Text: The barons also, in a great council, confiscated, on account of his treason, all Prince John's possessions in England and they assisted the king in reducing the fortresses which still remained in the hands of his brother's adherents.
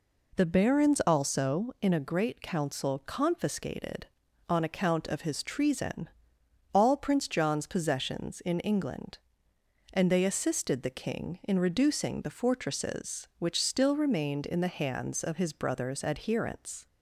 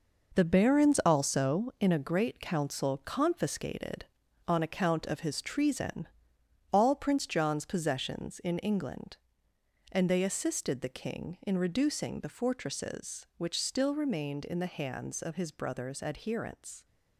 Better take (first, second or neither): first